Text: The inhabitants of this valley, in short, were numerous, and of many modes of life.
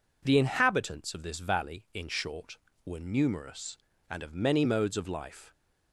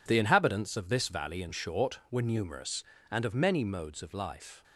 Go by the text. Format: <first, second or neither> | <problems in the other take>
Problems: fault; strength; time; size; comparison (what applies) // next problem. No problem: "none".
neither | none